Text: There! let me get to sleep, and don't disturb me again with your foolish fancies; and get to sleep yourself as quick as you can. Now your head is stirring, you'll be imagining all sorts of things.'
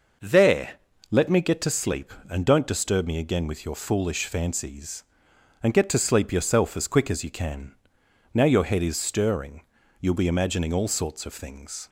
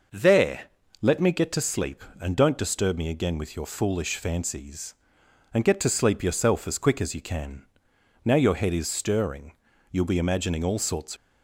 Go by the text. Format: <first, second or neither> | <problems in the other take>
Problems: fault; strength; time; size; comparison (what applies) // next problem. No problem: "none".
first | stops before "of things"; at 11.1 s